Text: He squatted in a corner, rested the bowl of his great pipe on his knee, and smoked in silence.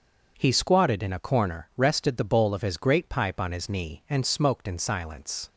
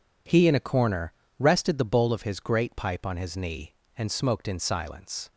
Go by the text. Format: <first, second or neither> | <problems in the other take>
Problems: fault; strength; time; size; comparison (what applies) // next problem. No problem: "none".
first | skips "squatted"; at 0.4 s